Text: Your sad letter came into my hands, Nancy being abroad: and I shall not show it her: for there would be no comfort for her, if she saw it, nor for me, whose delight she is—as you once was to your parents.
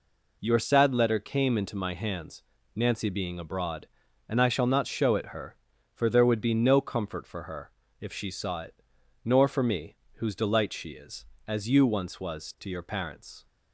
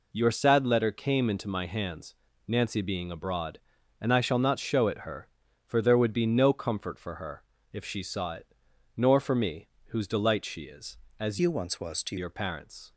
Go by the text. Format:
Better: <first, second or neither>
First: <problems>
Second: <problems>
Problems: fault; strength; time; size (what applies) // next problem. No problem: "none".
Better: first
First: none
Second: changes voice from "you" to "to"; from 11.3 to 12.1 s; 0.8 s long